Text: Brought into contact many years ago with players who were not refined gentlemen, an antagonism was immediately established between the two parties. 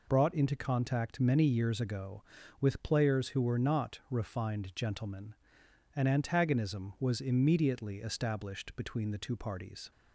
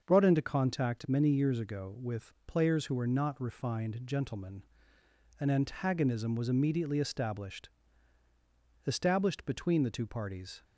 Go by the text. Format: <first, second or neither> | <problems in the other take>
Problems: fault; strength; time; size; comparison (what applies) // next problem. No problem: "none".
first | starts louder than the rest; until 1.0 s; 6.5 dB // pauses between "with" and "players"; slight; at 2.3 s; 0.16 s long // says "established" twice; at 8.8 s